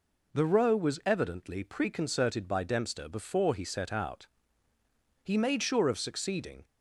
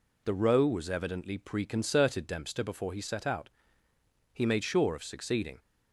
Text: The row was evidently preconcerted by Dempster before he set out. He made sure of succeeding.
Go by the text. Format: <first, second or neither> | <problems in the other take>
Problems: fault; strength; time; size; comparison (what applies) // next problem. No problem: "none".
first | skips "by"; at 2.2 s